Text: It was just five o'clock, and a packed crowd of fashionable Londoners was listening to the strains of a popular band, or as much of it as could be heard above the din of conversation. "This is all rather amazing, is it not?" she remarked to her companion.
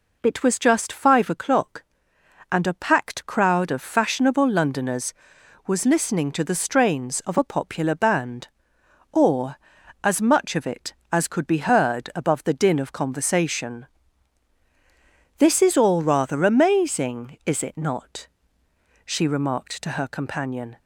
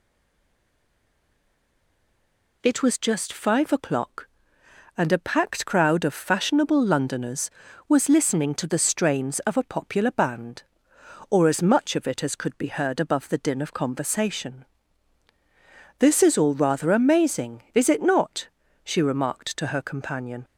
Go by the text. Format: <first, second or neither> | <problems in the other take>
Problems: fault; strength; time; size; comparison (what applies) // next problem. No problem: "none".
first | stays silent before the first word; strong; until 2.6 s; 2.6 s long